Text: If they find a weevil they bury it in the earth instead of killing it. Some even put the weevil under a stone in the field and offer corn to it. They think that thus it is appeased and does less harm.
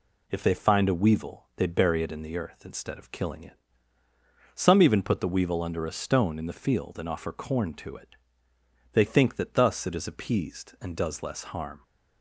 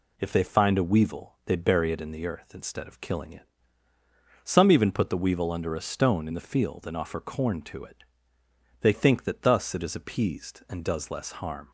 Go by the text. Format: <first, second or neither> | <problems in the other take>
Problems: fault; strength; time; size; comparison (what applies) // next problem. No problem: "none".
neither | none